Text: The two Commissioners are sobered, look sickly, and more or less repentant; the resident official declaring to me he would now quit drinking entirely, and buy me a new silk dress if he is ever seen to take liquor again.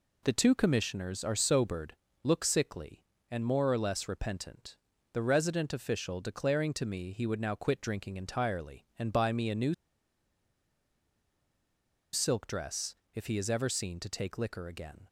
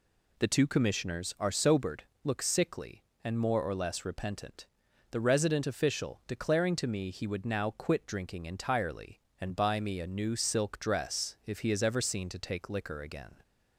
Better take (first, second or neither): second